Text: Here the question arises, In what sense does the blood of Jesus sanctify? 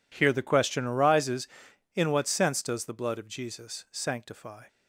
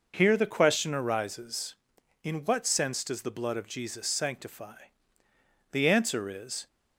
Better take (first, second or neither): first